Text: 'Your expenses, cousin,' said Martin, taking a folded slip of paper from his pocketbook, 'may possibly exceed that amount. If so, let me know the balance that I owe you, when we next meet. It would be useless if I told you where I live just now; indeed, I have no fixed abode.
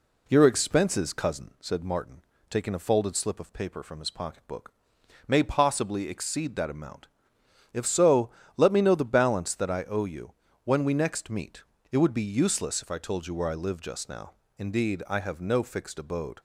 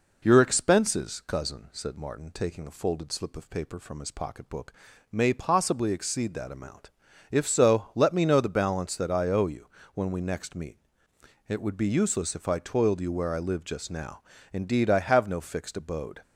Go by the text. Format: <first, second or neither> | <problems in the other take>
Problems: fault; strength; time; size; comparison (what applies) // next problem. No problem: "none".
first | says "toiled" for "told"; at 12.5 s